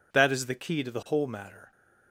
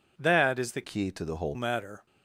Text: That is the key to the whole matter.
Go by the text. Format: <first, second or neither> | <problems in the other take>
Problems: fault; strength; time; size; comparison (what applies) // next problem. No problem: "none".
first | changes voice from "key" to "whole"; from 0.8 to 1.5 s; 0.7 s long